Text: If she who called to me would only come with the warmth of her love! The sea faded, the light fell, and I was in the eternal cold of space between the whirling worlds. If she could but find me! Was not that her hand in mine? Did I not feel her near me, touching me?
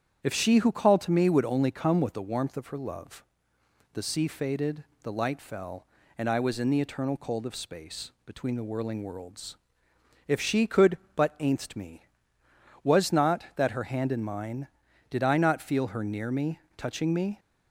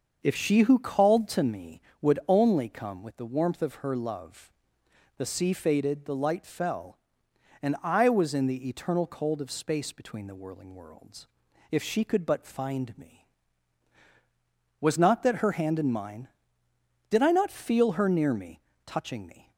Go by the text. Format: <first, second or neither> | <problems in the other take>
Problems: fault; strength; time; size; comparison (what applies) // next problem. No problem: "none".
second | starts louder than the rest; strong; until 1.2 s; 9 dB; also in the second // says "ainst" for "find"; at 11.3 s